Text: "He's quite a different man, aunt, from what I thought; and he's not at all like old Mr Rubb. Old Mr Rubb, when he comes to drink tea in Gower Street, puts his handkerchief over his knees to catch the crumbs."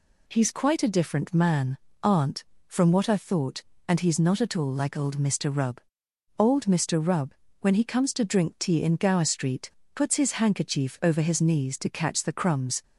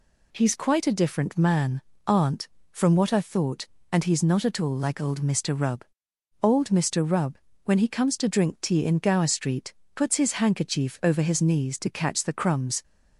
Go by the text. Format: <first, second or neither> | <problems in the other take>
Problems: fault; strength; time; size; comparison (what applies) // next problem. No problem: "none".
neither | none